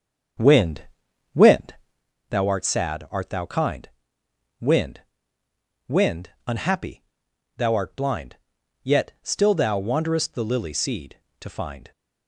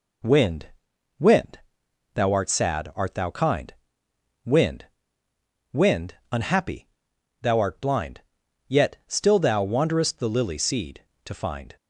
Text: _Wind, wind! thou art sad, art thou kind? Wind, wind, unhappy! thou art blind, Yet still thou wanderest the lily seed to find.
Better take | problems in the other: second | starts louder than the rest; strong; until 2.2 s; 7 dB

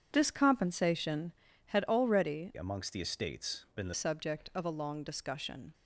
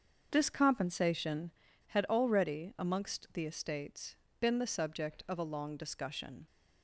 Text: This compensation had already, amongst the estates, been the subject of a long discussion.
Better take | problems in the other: second | starts louder than the rest; strong; until 1.1 s; 8 dB; also in the second // changes voice from "amongst" to "the"; from 2.5 to 3.9 s; 1.4 s long

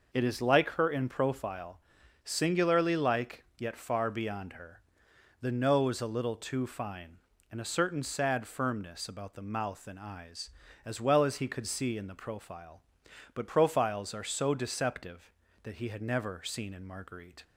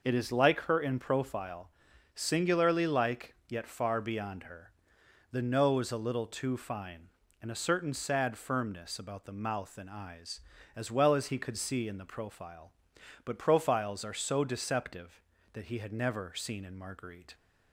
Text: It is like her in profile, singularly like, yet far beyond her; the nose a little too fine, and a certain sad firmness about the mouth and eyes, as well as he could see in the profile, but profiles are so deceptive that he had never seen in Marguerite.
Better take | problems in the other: neither | none

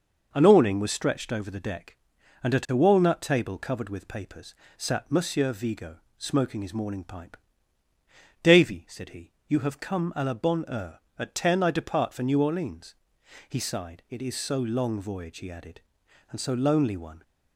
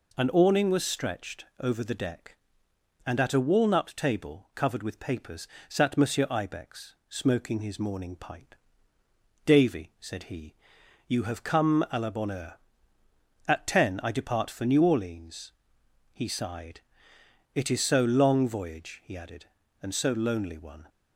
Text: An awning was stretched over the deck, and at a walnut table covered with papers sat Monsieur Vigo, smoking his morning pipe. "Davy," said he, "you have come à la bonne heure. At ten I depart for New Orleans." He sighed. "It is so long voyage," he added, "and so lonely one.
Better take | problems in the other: first | pauses between "papers" and "sat"; slight; at 5.4 s; 0.24 s long; slight in the first // says "Ibex" for "Vigo"; at 6.3 s

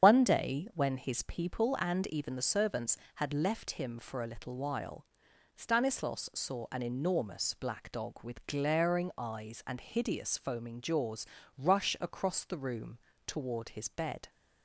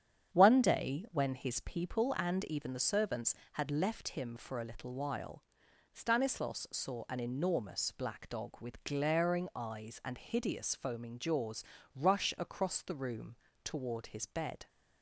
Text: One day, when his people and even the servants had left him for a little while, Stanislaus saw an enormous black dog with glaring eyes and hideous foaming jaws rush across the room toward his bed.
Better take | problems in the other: second | loses the start of "One"; at 0.0 s; 70 ms // starts louder than the rest; strong; until 1.1 s; 8 dB; strong in the second // pauses between "jaws" and "rush"; slight; at 11.2 s; 0.30 s long; slight in the second // pauses between "room" and "toward"; slight; at 12.9 s; 0.30 s long; slight in the second

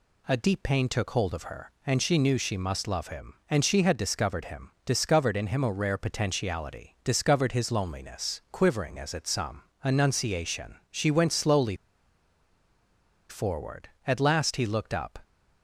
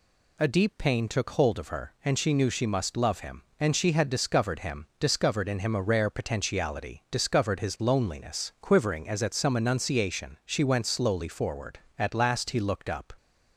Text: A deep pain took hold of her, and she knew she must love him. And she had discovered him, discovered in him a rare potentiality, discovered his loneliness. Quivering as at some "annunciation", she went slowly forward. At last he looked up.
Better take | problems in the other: second | pauses between "some" and "annunciation"; slight; at 9.6 s; 0.18 s long // pauses between "slowly" and "forward"; strong; at 11.7 s; 1.5 s long

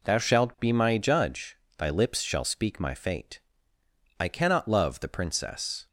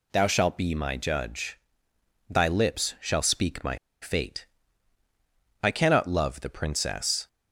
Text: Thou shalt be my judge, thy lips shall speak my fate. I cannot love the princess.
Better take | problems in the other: first | pauses between "my" and "fate"; slight; at 3.7 s; 0.25 s long

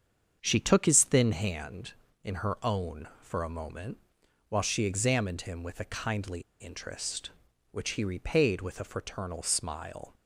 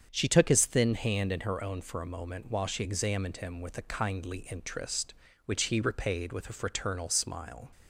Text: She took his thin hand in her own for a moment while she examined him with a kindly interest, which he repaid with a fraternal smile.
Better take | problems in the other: second | starts louder than the rest; strong; until 1.4 s; 7.5 dB; strong in the second // pauses between "moment" and "while"; noticeable; at 3.9 s; 0.50 s long // pauses between "kindly" and "interest"; slight; at 6.4 s; 0.19 s long

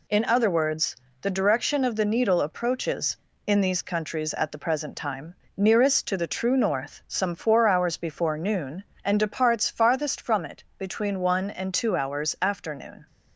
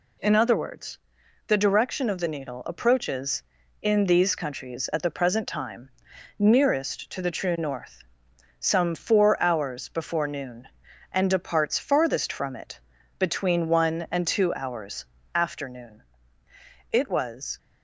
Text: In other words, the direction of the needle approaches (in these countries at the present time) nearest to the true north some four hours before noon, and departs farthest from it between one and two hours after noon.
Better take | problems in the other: first | pauses between "north" and "some"; noticeable; at 8.0 s; 0.56 s long // pauses between "it" and "between"; at 12.7 s; 0.40 s long; slight in the first // pauses between "hours" and "after"; slight; at 15.0 s; 0.28 s long // goes on to say "It was"; noticeable; from 16.9 s on; 0.66 s long

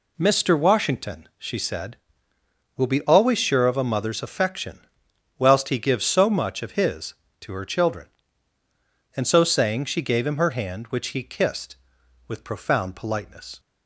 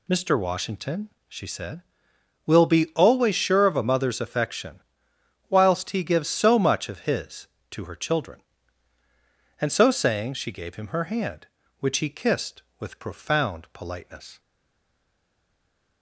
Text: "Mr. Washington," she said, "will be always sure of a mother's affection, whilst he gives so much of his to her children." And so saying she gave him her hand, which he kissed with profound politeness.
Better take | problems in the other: first | stays silent after the last word; noticeable; from 14.3 s on; 1.7 s long

